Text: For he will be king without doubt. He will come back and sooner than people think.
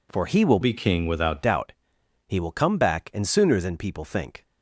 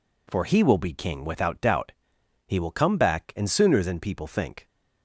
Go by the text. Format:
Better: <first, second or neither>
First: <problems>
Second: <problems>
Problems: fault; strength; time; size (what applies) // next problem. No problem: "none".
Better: second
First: changes voice from "be" to "without"; from 0.6 to 1.4 s; 0.8 s long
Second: none